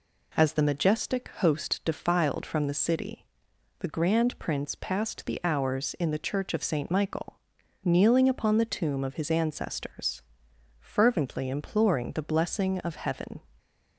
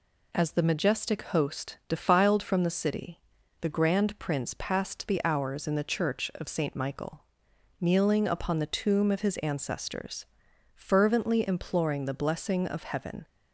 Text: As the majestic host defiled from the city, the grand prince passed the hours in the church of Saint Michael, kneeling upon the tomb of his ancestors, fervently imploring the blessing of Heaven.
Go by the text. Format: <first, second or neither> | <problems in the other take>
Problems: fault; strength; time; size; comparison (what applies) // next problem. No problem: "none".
neither | none